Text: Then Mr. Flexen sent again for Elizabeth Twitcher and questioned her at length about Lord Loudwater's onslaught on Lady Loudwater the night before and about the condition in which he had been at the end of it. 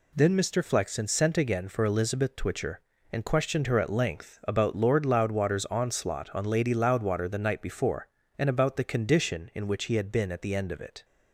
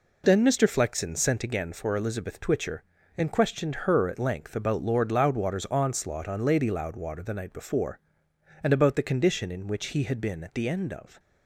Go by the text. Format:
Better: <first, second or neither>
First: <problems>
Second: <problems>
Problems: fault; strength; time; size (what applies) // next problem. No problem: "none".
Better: first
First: none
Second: stops before "it"; at 11.1 s